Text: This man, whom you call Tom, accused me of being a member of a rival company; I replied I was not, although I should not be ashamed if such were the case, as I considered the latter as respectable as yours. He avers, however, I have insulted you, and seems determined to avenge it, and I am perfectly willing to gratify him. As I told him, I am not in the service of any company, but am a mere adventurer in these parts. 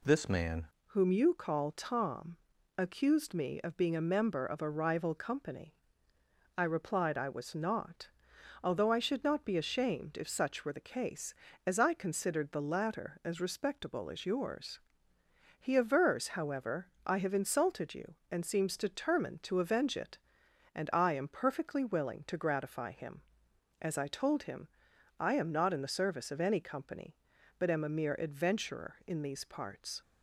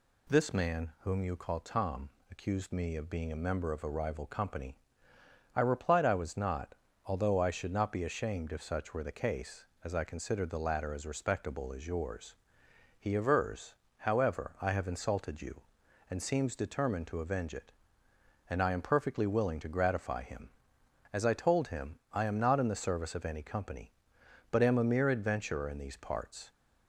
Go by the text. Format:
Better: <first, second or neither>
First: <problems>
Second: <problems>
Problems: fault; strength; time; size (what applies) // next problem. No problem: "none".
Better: second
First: changes voice at "whom"; from 0.8 s on; 29.2 s long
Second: none